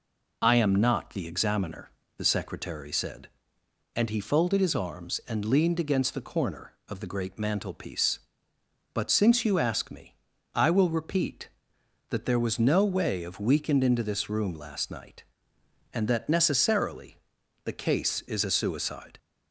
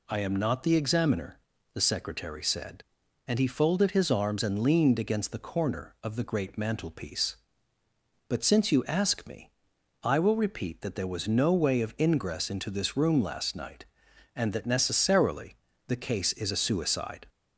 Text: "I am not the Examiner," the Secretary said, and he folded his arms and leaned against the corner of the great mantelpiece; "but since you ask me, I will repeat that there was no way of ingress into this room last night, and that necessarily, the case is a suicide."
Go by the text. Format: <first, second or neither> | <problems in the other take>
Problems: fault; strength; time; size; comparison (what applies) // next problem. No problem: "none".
second | says "weakened" for "ingress"; at 13.3 s